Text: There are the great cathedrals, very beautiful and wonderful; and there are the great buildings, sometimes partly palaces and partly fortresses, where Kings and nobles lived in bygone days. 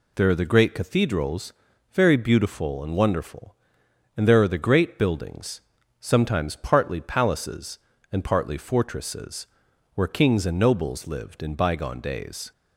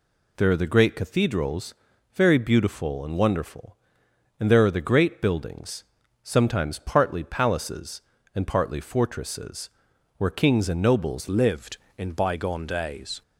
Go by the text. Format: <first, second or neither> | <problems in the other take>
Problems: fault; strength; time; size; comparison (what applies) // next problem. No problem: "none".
first | changes voice at "lived"; from 11.2 s on; 2.0 s long